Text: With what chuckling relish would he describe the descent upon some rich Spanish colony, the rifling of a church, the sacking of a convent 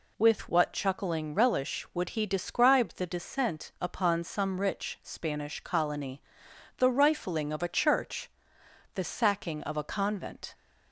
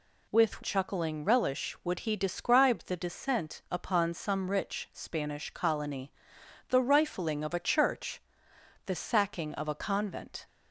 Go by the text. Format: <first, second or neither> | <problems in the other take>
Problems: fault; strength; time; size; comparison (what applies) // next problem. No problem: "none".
first | skips "what"; at 0.6 s